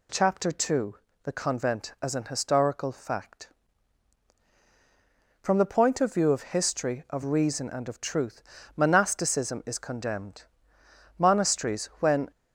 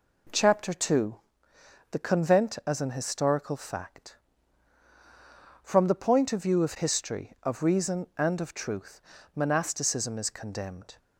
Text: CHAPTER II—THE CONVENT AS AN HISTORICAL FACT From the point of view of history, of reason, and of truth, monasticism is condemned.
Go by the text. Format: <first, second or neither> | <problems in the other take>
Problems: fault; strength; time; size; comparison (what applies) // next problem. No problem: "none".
second | goes on to say "Monasteries when"; noticeable; from 11.1 s on; 1.1 s long